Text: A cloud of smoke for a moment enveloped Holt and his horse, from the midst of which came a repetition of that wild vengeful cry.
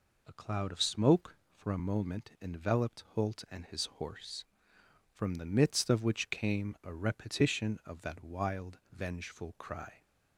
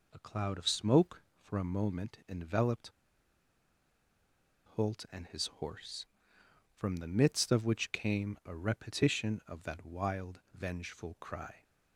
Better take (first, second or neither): first